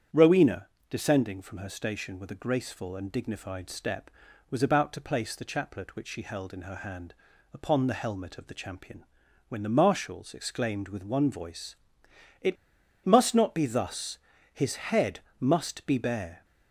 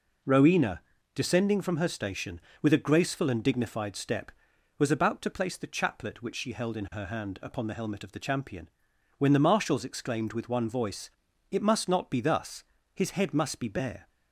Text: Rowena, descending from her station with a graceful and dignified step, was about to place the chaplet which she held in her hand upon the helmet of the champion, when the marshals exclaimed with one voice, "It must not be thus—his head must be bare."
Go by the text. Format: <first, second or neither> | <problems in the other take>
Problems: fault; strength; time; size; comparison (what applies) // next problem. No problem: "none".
second | starts louder than the rest; strong; until 1.3 s; 8.5 dB // pauses between "hand" and "upon"; at 7.1 s; 0.40 s long // pauses between "It" and "must"; noticeable; at 12.5 s; 0.50 s long // pauses between "head" and "must"; slight; at 15.1 s; 0.22 s long